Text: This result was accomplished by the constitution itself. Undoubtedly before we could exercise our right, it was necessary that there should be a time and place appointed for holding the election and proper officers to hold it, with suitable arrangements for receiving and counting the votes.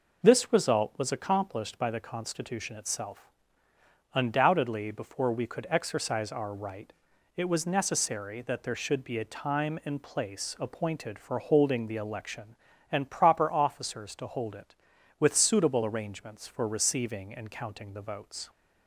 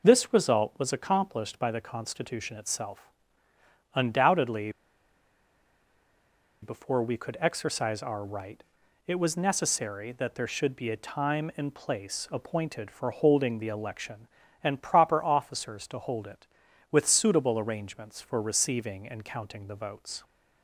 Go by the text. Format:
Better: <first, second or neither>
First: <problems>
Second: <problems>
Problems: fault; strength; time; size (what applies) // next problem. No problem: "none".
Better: first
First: none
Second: pauses between "Undoubtedly" and "before"; strong; at 4.7 s; 1.9 s long